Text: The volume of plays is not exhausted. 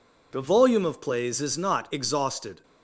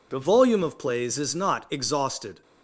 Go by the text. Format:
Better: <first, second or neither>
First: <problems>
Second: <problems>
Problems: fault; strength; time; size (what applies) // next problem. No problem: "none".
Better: neither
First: none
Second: none